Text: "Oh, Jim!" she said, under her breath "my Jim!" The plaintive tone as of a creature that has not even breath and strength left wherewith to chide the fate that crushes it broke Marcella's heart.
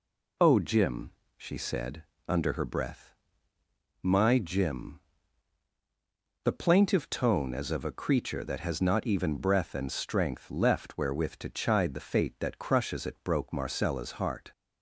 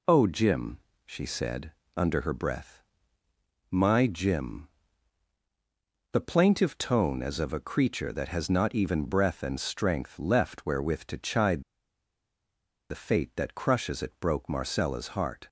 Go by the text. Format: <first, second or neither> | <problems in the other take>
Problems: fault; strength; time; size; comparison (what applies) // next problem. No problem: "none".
first | pauses between "breath" and "my"; noticeable; at 2.8 s; 0.88 s long; noticeable in the first // pauses between "chide" and "the"; strong; at 11.6 s; 1.2 s long